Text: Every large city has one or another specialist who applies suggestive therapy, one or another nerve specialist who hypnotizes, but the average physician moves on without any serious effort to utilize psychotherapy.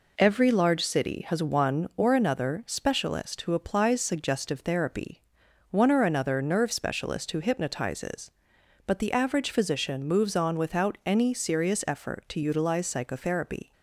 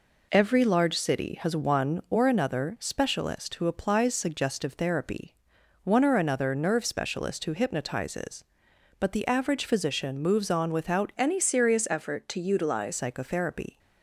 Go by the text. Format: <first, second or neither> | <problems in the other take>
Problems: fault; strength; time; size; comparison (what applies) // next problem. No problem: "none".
first | changes voice from "any" to "utilize"; from 11.1 to 12.9 s; 1.8 s long